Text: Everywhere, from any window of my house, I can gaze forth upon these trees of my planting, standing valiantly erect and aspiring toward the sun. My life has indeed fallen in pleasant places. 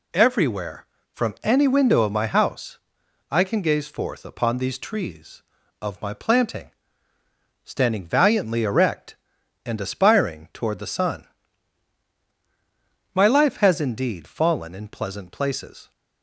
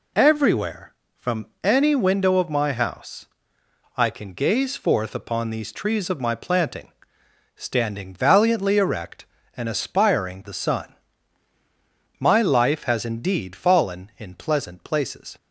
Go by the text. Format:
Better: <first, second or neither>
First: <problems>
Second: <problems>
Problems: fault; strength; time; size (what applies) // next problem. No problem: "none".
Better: first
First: none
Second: pauses between "from" and "any"; slight; at 1.4 s; 0.18 s long // skips "toward"; at 10.4 s